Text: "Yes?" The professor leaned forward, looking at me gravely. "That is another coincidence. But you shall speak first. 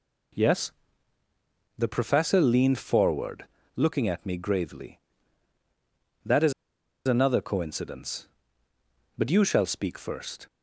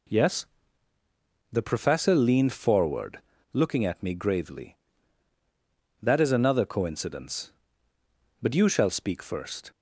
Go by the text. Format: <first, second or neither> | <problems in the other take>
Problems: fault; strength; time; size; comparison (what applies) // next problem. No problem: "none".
second | pauses between "is" and "another"; noticeable; at 6.5 s; 0.55 s long